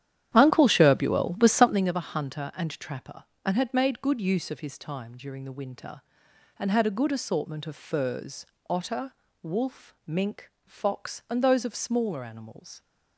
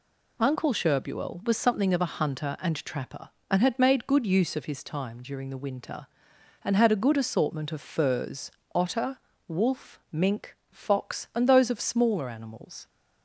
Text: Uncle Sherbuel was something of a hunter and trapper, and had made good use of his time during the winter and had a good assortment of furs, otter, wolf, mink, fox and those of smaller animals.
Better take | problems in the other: second | starts louder than the rest; strong; until 1.9 s; 10.5 dB

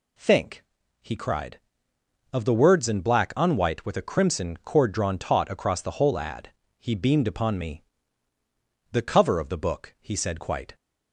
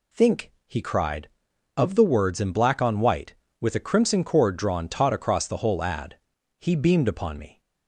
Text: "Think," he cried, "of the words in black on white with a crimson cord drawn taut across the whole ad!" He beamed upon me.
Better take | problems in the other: second | goes on to say "The cover of the book he said quite"; strong; from 8.9 s on; 1.8 s long

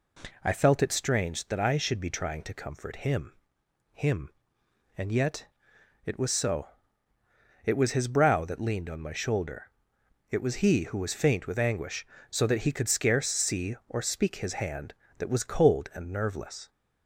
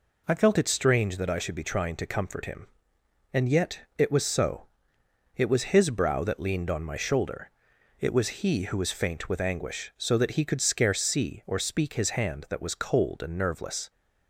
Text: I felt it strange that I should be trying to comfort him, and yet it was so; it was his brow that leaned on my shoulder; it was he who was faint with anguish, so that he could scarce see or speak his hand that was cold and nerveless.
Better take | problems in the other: second | says "him" twice; at 3.9 s // pauses between "yet" and "it"; noticeable; at 5.4 s; 0.60 s long; slight in the second

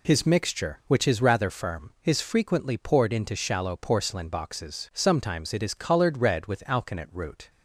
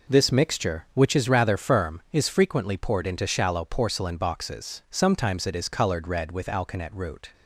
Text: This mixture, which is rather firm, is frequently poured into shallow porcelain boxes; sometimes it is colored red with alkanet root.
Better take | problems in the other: second | says "His" for "This"; at 0.0 s

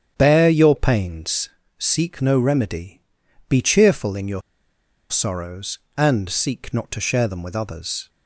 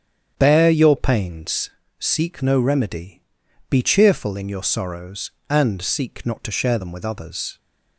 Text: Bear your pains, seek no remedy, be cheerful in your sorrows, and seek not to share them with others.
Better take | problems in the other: second | starts louder than the rest; strong; until 1.1 s; 8.5 dB; strong in the second // pauses between "your" and "sorrows"; noticeable; at 4.4 s; 0.69 s long

